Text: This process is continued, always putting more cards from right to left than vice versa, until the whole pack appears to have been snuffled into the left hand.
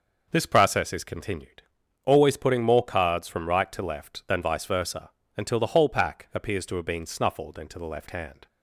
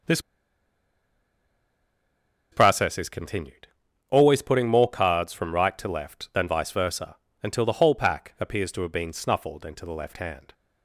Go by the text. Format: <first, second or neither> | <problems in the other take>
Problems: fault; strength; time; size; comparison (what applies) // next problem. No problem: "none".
first | pauses between "This" and "process"; strong; at 0.1 s; 2.3 s long